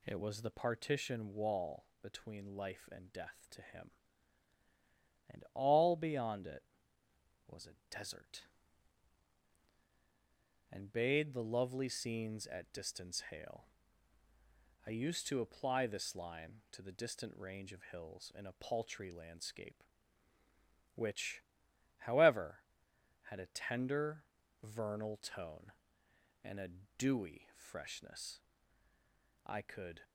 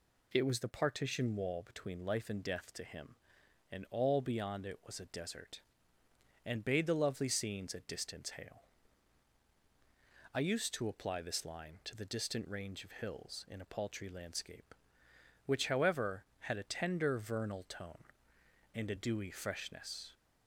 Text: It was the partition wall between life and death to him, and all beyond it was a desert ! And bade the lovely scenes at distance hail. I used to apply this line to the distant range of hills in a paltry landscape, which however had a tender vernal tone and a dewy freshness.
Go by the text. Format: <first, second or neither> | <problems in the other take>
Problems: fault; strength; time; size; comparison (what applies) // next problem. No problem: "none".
second | pauses between "wall" and "between"; slight; at 1.8 s; 0.16 s long // pauses between "which" and "however"; noticeable; at 21.4 s; 0.56 s long // pauses between "tender" and "vernal"; at 24.2 s; 0.38 s long // pauses between "a" and "dewy"; slight; at 26.6 s; 0.30 s long // goes on to say "I could"; from 29.4 s on; 0.58 s long